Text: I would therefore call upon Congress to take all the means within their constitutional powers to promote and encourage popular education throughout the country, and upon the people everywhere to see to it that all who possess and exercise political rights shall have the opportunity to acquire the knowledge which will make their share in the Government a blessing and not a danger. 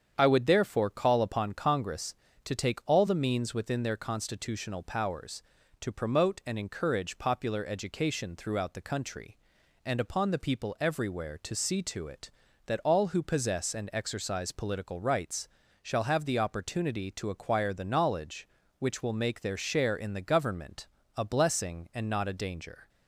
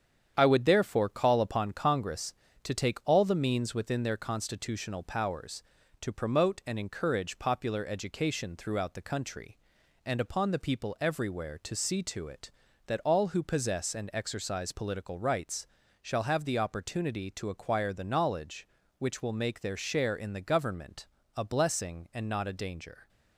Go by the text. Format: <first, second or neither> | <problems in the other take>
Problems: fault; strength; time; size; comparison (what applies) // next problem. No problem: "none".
first | gets quieter; noticeable; throughout; 5.5 dB // starts louder than the rest; strong; until 1.3 s; 8.5 dB; strong in the first // pauses between "rights" and "shall"; slight; at 15.6 s; 0.34 s long; slight in the first // pauses between "Government" and "a"; slight; at 21.0 s; 0.30 s long; slight in the first